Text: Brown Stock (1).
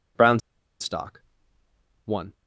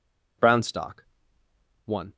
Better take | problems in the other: second | pauses between "Brown" and "Stock"; at 0.3 s; 0.42 s long

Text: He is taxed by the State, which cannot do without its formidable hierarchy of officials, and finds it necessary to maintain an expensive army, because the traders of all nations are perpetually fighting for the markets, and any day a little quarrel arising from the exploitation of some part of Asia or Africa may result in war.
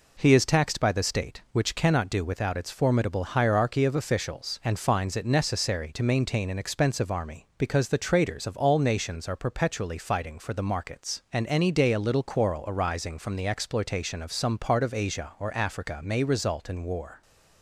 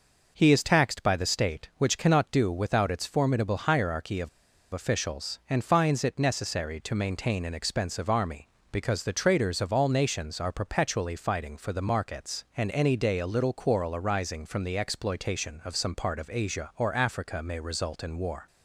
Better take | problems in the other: first | pauses between "of" and "officials"; at 4.2 s; 0.45 s long

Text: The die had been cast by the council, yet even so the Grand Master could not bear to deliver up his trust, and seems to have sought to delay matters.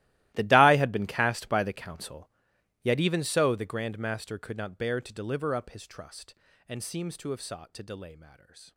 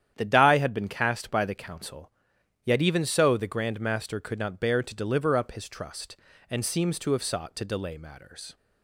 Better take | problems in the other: second | gets quieter; strong; throughout; 19.5 dB // starts louder than the rest; strong; until 1.3 s; 16.5 dB; strong in the second

